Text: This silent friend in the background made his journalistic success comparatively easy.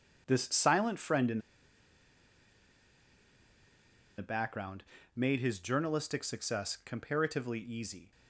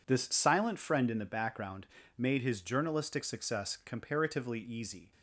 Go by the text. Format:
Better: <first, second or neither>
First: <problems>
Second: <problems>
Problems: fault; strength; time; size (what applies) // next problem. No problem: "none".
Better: second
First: pauses between "in" and "the"; strong; at 1.3 s; 2.7 s long // pauses between "background" and "made"; slight; at 4.8 s; 0.32 s long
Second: pauses between "background" and "made"; slight; at 1.8 s; 0.31 s long